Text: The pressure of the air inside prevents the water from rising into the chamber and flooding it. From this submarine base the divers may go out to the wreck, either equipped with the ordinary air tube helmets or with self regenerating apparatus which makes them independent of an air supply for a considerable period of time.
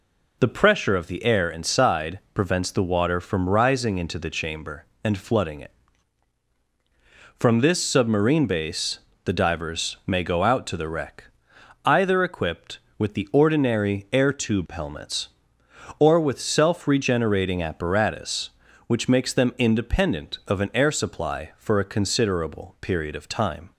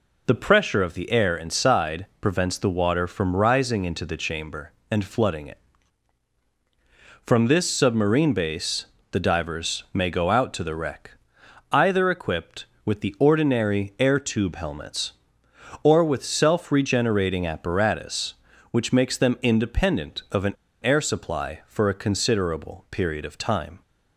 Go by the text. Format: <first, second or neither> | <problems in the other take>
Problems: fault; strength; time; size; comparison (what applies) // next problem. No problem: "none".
first | pauses between "base" and "the"; slight; at 8.8 s; 0.26 s long; slight in the first // pauses between "an" and "air"; slight; at 20.5 s; 0.27 s long